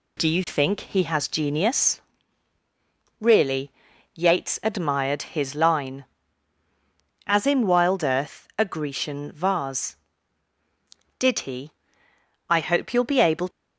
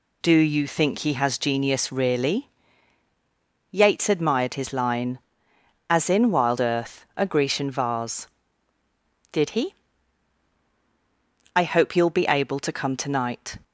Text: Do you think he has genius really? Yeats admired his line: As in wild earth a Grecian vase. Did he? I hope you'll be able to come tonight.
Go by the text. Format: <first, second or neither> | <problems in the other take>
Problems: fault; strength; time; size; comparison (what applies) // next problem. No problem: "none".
second | pauses between "genius" and "really"; at 1.9 s; 1.2 s long // stops before "to come tonight"; at 13.4 s